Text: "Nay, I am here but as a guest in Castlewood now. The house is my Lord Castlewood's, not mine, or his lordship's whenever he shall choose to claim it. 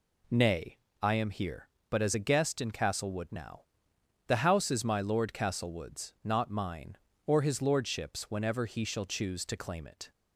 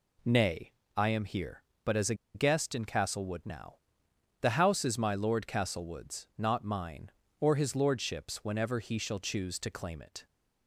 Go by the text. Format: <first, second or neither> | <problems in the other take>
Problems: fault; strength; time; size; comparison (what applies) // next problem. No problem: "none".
first | pauses between "a" and "guest"; slight; at 2.1 s; 0.20 s long